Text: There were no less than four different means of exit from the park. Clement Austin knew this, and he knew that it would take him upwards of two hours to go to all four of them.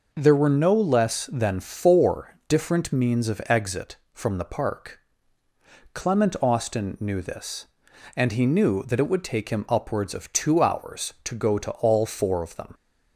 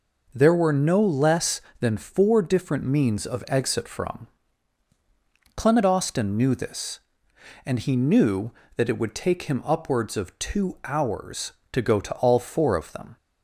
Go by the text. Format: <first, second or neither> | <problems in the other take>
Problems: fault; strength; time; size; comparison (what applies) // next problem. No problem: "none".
first | skips "the park"; at 4.9 s